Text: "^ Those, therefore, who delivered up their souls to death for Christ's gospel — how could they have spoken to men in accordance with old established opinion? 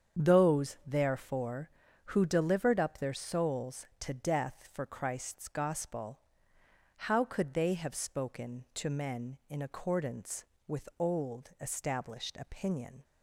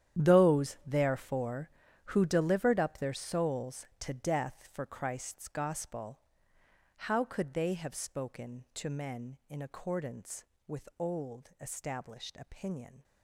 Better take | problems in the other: first | gets quieter; strong; throughout; 15.5 dB // starts louder than the rest; strong; until 1.2 s; 10.5 dB; strong in the first

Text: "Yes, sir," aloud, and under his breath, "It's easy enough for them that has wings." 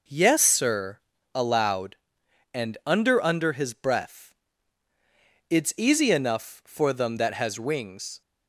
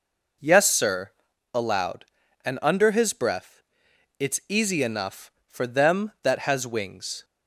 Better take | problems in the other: second | says "under" twice; at 3.2 s

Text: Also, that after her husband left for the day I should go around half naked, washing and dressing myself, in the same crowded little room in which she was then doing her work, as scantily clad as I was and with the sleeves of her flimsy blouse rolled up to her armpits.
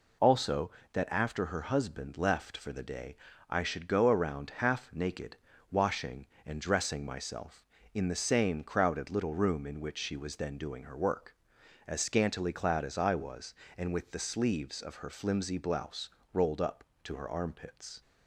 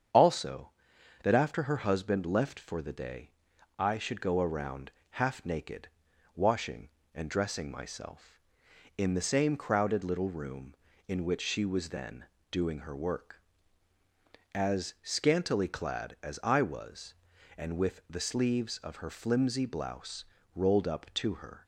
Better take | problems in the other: first | starts louder than the rest; strong; until 1.6 s; 8 dB // pauses between "day" and "I"; noticeable; at 3.3 s; 0.46 s long; slight in the first // pauses between "around" and "half"; slight; at 4.9 s; 0.20 s long // pauses between "then" and "doing"; slight; at 12.2 s; 0.26 s long // pauses between "blouse" and "rolled"; slight; at 20.2 s; 0.30 s long; slight in the first // stops before "armpits"; at 21.6 s

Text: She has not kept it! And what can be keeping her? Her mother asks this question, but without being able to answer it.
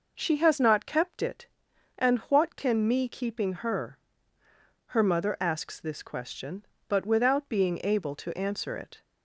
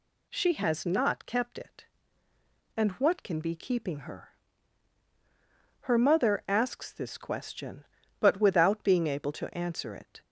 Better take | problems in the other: second | says "me" for "be"; at 2.8 s

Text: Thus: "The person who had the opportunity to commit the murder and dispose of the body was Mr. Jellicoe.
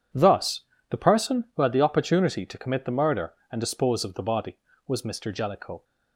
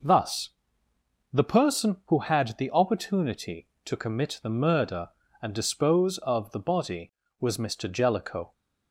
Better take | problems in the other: neither | none

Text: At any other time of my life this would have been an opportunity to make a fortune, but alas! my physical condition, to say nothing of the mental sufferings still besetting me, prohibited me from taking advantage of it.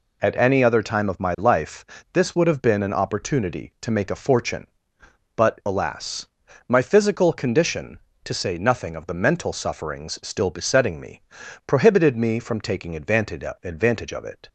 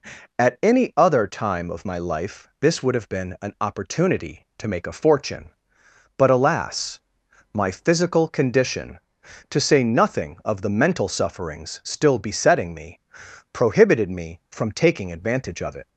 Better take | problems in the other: second | pauses between "life" and "this"; slight; at 1.8 s; 0.30 s long // says "advantage" twice; at 13.6 s

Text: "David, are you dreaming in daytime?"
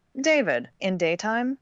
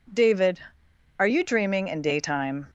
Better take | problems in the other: second | skips "are you dreaming"; at 0.7 s

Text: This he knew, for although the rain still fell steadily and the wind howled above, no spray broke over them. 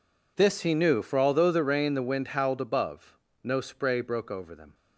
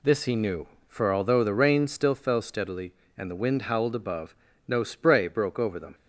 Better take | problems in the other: second | skips "still fell steadily and"; at 1.9 s

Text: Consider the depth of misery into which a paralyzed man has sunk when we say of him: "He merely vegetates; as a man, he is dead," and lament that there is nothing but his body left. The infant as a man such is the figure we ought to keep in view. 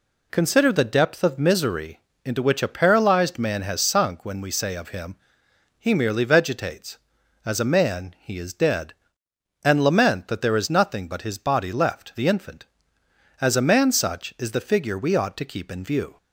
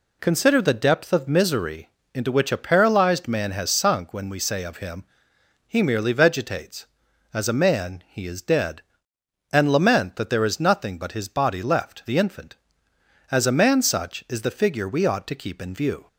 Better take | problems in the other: neither | pauses between "misery" and "into"; slight; the same in both

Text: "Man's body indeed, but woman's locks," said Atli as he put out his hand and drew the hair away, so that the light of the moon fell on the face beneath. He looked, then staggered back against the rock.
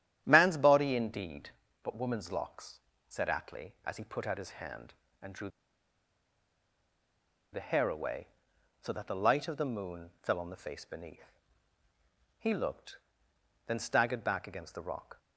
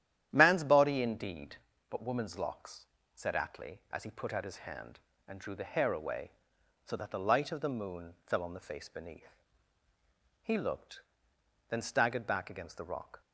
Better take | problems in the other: second | starts louder than the rest; strong; until 1.2 s; 11 dB; strong in the second // pauses between "drew" and "the"; strong; at 5.4 s; 2.0 s long

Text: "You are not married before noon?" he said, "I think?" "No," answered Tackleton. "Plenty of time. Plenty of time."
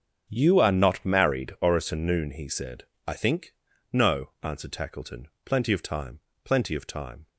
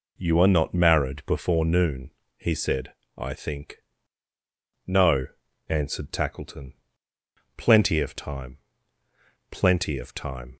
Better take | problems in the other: second | starts louder than the rest; until 1.3 s; 7 dB // says "orison" for "before"; at 1.6 s

